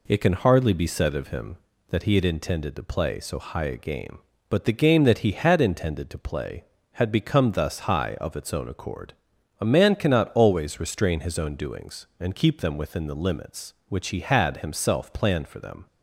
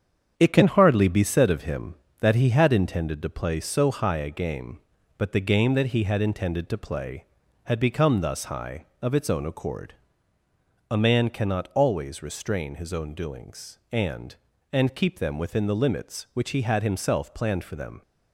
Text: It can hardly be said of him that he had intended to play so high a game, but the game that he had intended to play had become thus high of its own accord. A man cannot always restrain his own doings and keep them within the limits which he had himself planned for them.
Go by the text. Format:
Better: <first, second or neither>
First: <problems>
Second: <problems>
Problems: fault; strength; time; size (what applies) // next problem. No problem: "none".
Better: first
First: none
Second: starts louder than the rest; strong; until 1.3 s; 7.5 dB // says "and" twice; at 14.7 s